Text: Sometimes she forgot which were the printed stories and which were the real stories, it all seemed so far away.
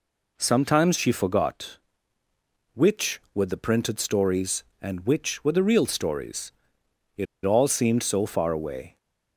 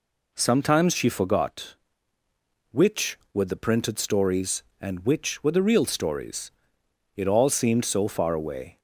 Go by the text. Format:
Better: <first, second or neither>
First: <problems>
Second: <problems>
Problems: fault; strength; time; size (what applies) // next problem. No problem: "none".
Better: second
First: pauses between "it" and "all"; slight; at 7.2 s; 0.19 s long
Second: none